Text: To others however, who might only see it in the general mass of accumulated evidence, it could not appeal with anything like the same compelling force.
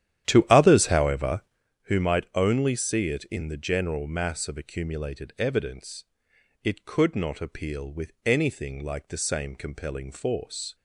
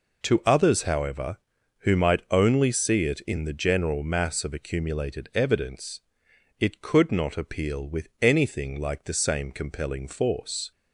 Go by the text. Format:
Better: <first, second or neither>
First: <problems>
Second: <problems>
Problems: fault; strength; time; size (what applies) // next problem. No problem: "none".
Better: second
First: starts louder than the rest; strong; until 1.7 s; 11 dB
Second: none